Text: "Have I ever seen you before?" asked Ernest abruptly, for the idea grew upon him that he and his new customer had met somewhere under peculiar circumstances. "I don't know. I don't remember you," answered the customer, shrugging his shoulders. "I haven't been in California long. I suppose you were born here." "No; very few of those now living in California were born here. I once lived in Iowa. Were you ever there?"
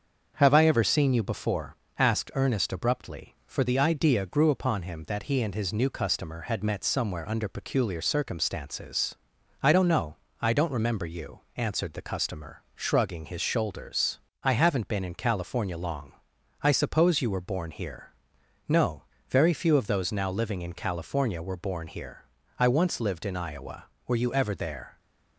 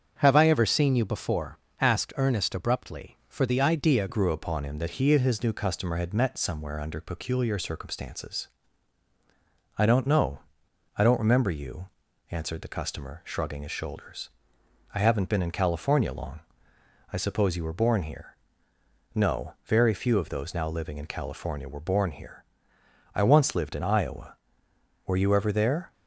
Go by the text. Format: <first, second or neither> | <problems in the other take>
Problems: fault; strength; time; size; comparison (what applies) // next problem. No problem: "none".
first | starts louder than the rest; strong; until 1.2 s; 7 dB; also in the first // changes voice at "grew"; from 4.0 s on; 21.9 s long